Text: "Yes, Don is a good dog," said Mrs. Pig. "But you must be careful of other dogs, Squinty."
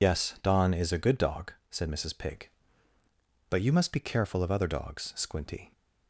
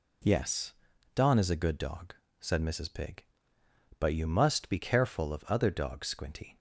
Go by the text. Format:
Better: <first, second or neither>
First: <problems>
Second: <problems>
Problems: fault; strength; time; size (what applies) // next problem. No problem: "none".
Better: second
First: loses the start of "Yes"; at 0.0 s; 110 ms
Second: none